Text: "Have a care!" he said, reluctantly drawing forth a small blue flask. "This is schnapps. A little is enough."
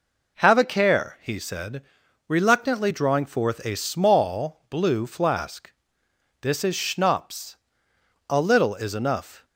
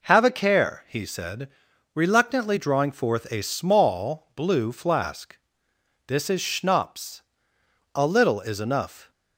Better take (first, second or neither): neither